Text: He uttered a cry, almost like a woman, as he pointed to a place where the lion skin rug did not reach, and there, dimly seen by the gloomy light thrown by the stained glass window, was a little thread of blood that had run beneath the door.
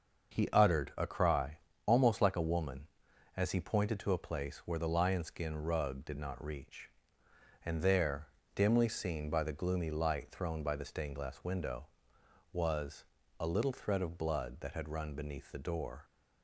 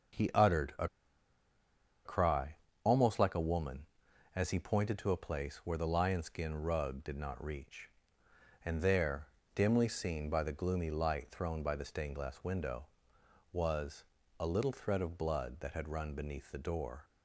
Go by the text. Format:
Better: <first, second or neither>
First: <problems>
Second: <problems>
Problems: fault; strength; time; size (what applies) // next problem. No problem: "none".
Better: first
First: starts louder than the rest; until 1.4 s; 6.5 dB // pauses between "was" and "a"; at 13.0 s; 0.38 s long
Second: starts louder than the rest; until 2.4 s; 6.5 dB // pauses between "a" and "cry"; at 0.8 s; 1.1 s long // pauses between "was" and "a"; at 14.0 s; 0.38 s long